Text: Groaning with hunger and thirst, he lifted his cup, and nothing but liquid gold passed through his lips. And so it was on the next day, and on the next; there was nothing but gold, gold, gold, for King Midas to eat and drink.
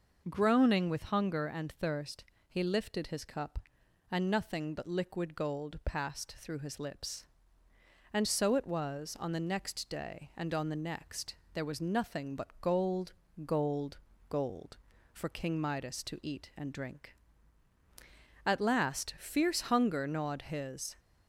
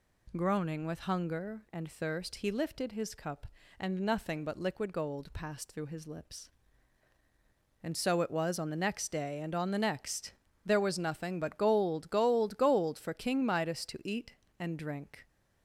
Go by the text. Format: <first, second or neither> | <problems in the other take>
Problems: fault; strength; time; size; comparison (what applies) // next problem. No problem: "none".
second | goes on to say "At last fierce hunger gnawed his"; strong; from 18.4 s on; 2.5 s long